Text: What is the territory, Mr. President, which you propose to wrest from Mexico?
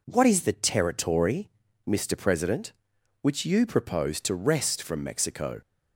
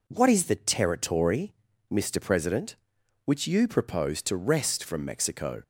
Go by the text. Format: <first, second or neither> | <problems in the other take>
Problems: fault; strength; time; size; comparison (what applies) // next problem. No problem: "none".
neither | none